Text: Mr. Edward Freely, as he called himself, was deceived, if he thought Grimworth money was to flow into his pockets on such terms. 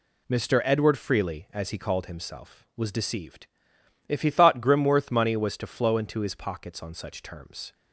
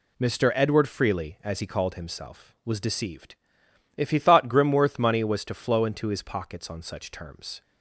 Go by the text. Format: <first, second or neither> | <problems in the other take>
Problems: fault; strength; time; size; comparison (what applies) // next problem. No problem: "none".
neither | none